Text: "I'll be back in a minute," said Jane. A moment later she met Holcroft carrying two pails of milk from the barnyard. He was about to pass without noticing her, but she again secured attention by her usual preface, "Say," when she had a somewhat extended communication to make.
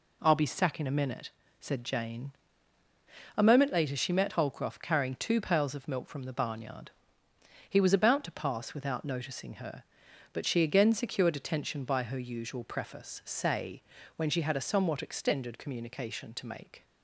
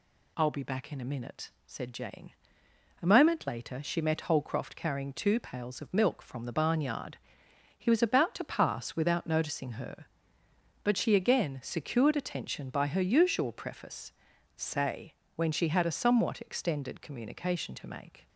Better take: second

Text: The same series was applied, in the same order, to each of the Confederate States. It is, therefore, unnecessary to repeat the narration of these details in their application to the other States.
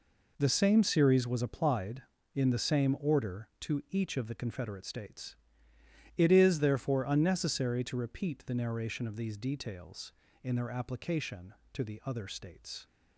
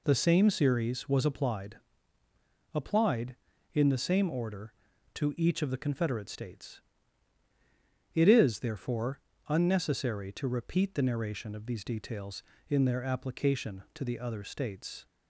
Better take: first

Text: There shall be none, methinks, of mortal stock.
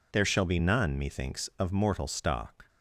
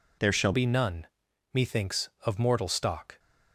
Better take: first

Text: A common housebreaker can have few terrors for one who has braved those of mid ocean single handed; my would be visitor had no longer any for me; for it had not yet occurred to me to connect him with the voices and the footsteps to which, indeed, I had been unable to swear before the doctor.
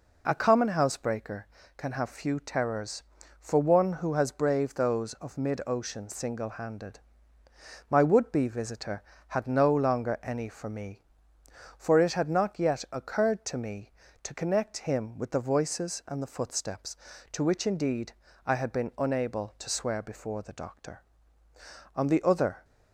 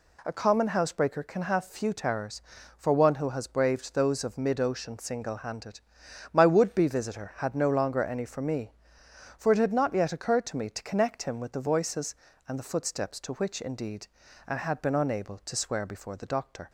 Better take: second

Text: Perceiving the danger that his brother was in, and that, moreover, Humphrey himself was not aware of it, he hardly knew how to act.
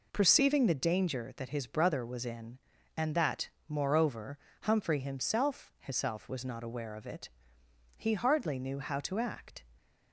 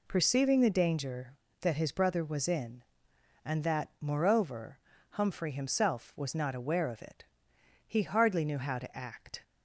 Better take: second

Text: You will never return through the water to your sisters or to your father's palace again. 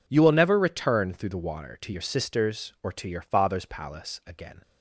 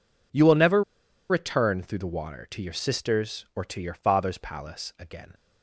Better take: first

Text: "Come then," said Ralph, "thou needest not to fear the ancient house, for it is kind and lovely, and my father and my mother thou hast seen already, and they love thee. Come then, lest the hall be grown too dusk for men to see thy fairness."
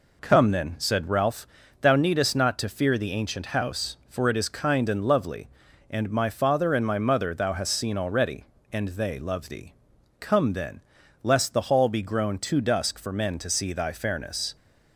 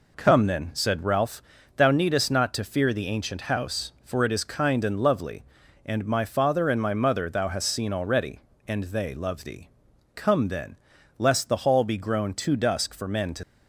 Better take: first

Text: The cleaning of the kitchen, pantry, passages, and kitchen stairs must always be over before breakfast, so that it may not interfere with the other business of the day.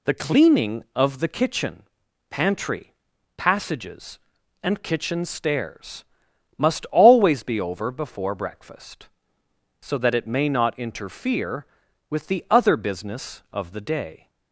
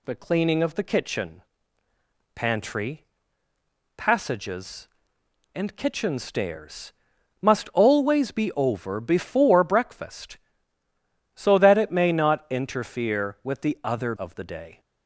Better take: first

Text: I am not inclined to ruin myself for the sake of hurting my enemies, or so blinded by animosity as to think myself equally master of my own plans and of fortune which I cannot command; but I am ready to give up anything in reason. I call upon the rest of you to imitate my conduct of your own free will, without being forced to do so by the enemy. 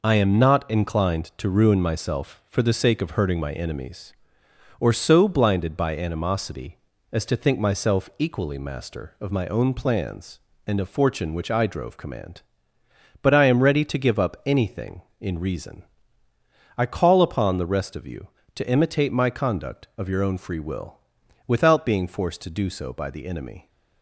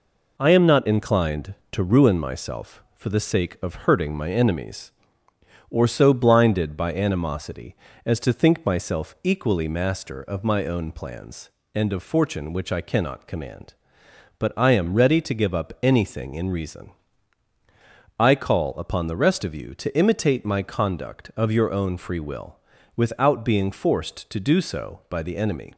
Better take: second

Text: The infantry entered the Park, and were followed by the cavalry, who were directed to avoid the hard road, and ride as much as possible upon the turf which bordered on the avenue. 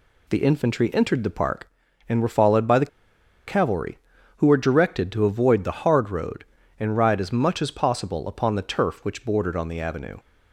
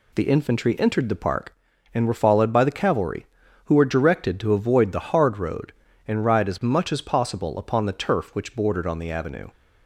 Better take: second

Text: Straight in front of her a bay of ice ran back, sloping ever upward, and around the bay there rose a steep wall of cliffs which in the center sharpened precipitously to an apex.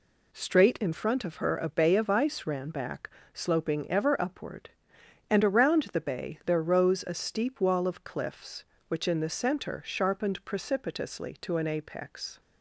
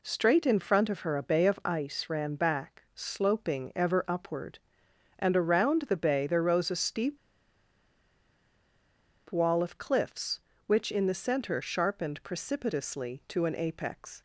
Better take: first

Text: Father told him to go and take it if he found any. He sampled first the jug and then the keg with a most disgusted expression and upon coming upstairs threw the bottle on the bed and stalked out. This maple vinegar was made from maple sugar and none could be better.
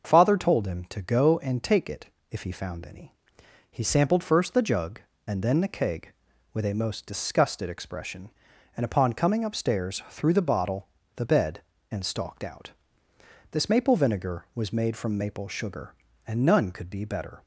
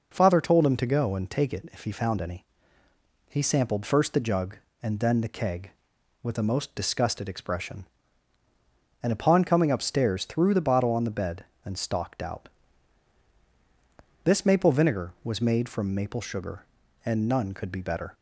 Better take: second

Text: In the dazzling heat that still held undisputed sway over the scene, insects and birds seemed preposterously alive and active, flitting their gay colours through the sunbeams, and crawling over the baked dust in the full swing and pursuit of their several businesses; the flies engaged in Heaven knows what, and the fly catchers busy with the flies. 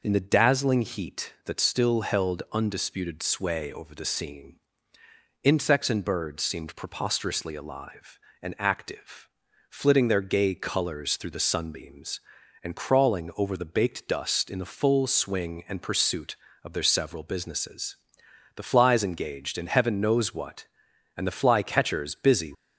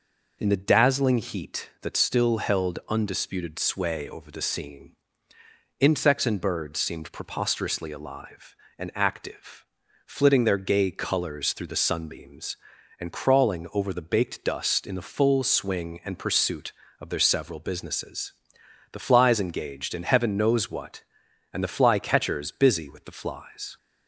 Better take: second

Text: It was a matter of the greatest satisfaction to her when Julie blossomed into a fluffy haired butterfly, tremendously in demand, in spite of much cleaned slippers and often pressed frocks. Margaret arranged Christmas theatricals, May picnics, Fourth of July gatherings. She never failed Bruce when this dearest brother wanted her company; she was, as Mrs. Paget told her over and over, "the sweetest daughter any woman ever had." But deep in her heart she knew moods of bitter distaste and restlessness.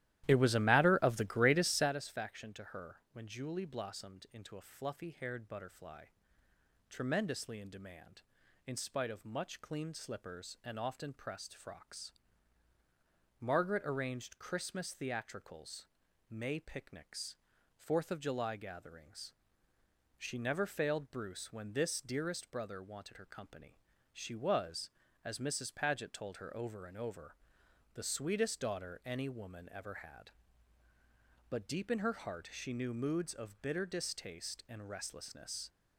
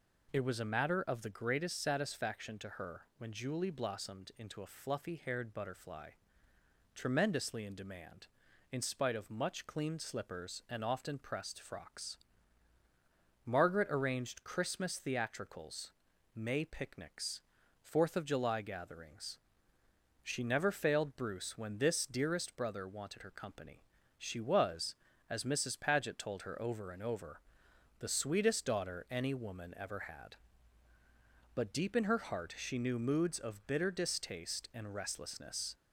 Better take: second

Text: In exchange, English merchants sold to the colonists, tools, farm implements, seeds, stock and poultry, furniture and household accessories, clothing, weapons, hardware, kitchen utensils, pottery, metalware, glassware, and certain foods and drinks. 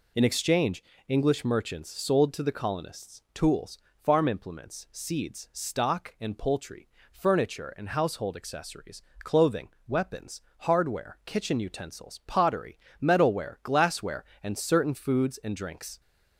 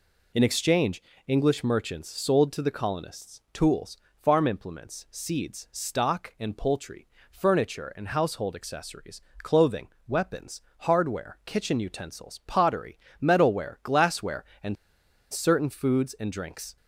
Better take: first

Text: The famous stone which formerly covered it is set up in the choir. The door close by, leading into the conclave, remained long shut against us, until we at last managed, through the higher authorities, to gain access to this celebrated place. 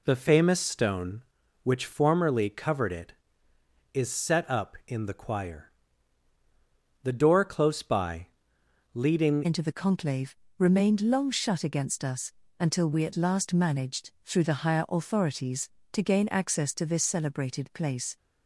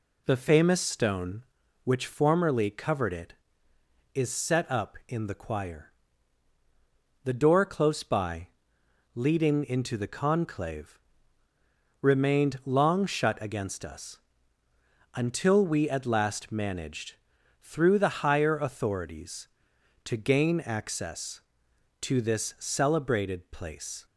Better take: second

